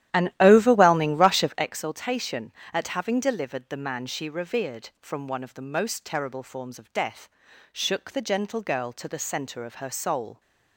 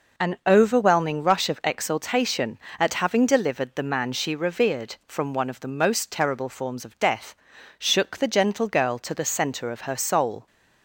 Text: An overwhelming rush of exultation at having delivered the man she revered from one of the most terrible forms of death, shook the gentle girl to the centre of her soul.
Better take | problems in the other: second | starts louder than the rest; strong; until 1.7 s; 12.5 dB

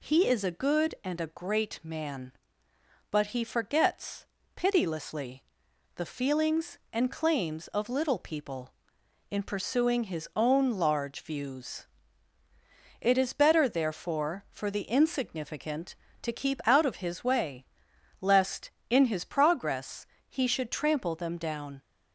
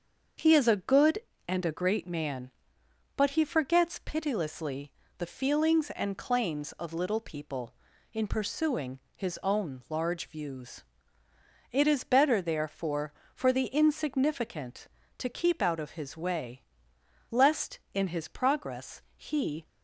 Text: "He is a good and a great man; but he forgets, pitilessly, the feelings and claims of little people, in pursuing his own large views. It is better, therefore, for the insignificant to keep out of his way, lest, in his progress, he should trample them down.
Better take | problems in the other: first | starts louder than the rest; until 1.6 s; 6.5 dB // pauses between "pursuing" and "his"; slight; at 9.0 s; 0.16 s long // stops before "should trample them down"; at 19.6 s

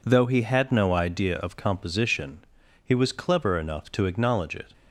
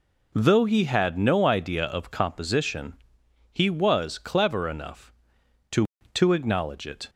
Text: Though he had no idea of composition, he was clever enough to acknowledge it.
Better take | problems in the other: first | says "to" twice; at 6.1 s

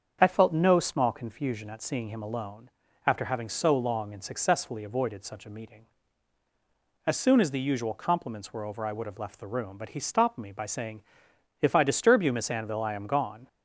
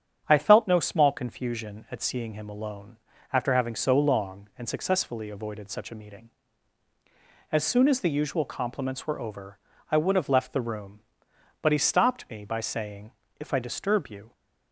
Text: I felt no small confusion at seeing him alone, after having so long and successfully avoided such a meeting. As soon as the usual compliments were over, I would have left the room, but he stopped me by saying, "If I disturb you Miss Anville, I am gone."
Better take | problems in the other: first | starts louder than the rest; strong; until 1.2 s; 8 dB; also in the first // stops before "Miss Anville I am gone"; at 14.3 s

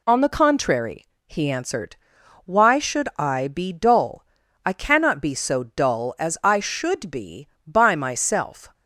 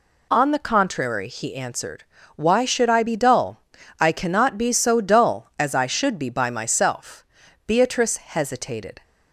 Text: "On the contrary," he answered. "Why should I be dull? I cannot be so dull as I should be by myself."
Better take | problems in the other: first | goes on to say "Beatrice hesitated"; from 7.6 s on; 1.3 s long

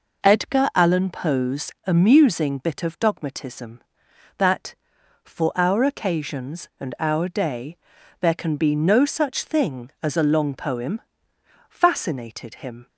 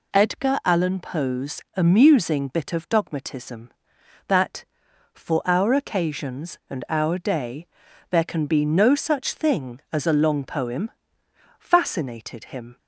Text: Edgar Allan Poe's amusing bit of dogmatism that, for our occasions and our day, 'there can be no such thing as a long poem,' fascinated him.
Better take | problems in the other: second | starts louder than the rest; noticeable; until 1.9 s; 5 dB // pauses between "Poe's" and "amusing"; slight; at 1.7 s; 0.16 s long; slight in the second

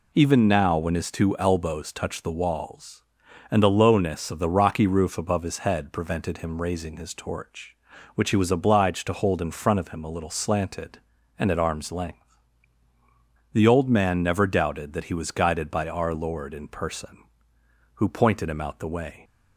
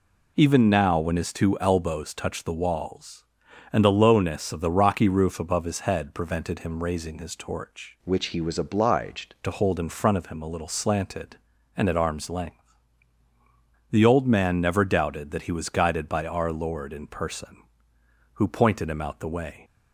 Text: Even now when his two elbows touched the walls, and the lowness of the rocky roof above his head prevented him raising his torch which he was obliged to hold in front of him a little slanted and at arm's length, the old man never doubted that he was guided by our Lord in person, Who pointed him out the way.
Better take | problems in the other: first | changes voice from "which" to "obliged"; from 8.0 to 9.3 s; 1.3 s long

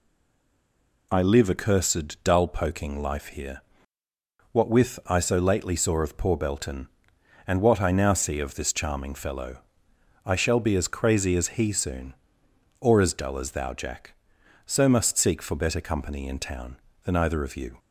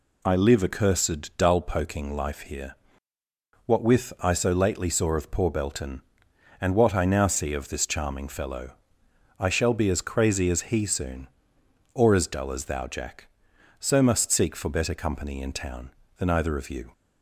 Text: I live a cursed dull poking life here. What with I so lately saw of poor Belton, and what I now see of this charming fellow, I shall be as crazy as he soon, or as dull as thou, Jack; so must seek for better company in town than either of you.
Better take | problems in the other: second | stays silent before the first word; until 1.1 s; 1.1 s long

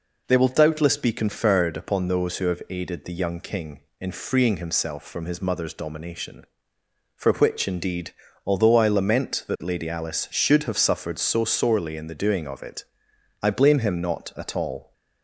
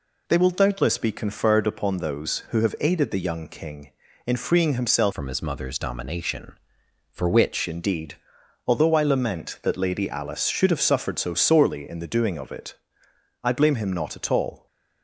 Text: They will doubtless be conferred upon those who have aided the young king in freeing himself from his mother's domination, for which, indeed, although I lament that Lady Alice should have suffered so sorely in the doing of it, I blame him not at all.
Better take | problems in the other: first | changes voice from "from" to "which"; from 5.1 to 7.6 s; 2.5 s long

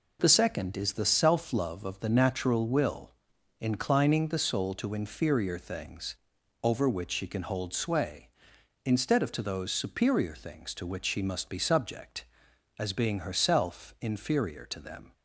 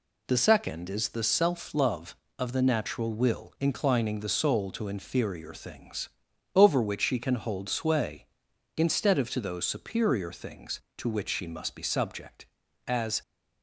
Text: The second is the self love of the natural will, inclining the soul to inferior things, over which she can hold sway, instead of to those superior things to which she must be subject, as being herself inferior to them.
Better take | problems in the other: first | stops before "being herself inferior to them"; at 13.2 s

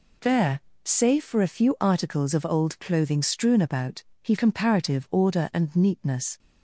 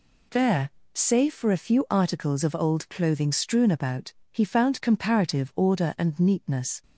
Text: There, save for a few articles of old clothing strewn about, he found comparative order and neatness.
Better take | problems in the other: second | skips "found"; at 4.3 s

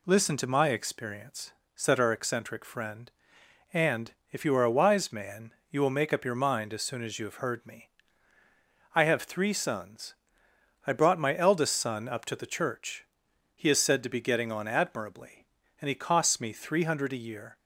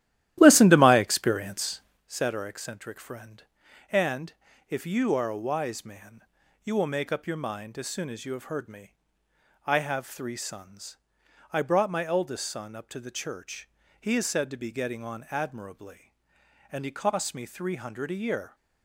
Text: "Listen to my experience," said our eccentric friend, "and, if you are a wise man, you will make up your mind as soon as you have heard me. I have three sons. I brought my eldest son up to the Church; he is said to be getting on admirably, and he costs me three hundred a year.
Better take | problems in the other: first | starts louder than the rest; strong; until 2.1 s; 13.5 dB

